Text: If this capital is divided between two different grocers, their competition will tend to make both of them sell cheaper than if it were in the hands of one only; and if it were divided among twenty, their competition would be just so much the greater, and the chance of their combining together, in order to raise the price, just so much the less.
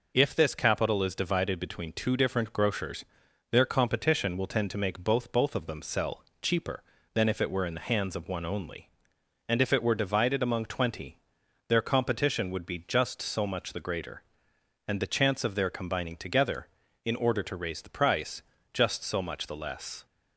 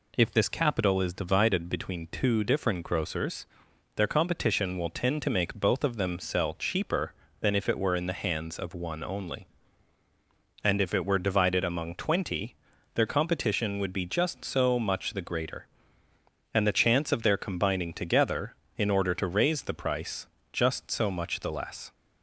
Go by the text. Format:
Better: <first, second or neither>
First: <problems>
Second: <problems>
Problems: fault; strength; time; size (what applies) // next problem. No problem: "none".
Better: second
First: says "both" twice; at 5.3 s // pauses between "sell" and "cheaper"; slight; at 6.2 s; 0.18 s long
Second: none